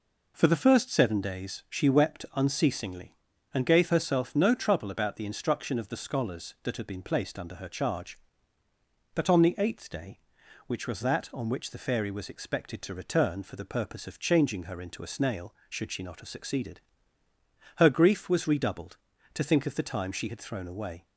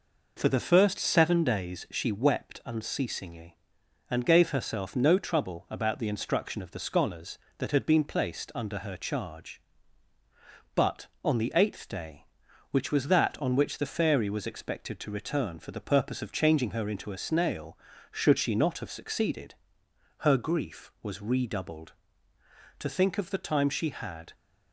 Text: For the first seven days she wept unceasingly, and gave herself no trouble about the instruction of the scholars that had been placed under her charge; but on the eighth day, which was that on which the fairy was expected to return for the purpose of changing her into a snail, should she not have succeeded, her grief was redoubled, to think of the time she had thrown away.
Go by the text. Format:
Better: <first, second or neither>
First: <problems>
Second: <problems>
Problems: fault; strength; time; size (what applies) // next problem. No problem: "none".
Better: first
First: none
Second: stops before "thrown away"; at 24.3 s